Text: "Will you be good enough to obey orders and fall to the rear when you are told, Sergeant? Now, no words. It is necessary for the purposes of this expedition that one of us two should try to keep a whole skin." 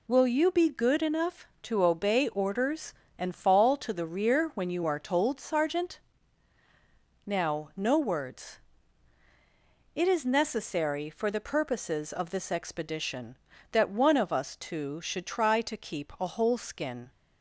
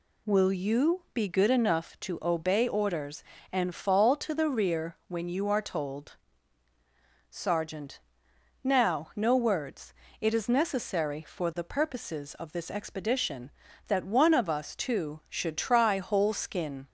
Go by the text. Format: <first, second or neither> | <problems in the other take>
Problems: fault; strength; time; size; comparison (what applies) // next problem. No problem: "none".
first | skips "to keep a"; at 15.9 s